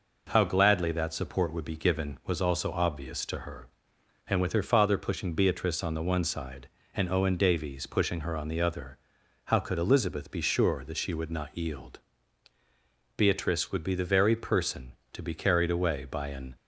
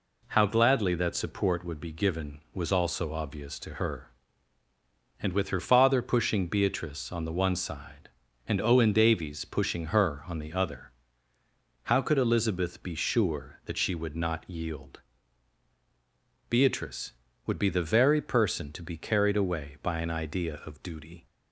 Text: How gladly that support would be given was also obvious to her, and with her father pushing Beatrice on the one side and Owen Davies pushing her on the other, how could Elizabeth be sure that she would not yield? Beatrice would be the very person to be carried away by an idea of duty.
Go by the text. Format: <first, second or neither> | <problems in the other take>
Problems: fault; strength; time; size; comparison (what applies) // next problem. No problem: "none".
second | stops before "idea of duty"; at 16.5 s